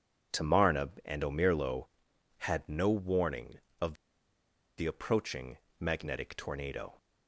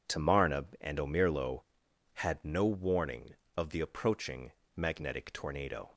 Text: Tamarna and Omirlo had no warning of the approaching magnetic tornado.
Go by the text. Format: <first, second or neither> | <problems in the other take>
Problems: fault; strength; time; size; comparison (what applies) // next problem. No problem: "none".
second | pauses between "of" and "the"; noticeable; at 3.9 s; 0.83 s long // pauses between "approaching" and "magnetic"; slight; at 5.5 s; 0.20 s long; slight in the second